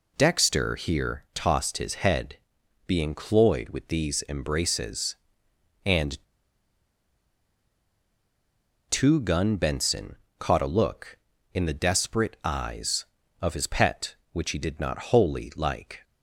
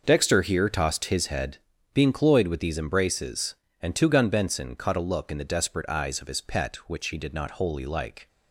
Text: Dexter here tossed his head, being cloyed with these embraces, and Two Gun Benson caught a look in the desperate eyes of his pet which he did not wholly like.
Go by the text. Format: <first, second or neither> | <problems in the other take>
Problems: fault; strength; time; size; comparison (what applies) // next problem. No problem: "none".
second | pauses between "and" and "Two"; strong; at 6.1 s; 2.7 s long // pauses between "Benson" and "caught"; slight; at 10.1 s; 0.22 s long